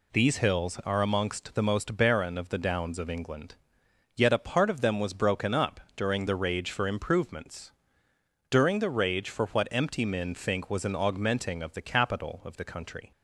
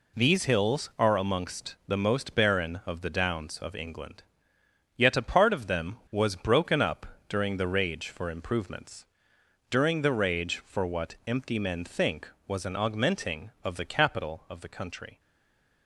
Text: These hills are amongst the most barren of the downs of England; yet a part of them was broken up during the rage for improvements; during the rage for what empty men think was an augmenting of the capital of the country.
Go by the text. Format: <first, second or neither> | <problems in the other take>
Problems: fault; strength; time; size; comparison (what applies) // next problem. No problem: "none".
first | pauses between "up" and "during"; slight; at 7.0 s; 0.22 s long; slight in the first // stays silent after the last word; slight; from 15.1 s on; 0.7 s long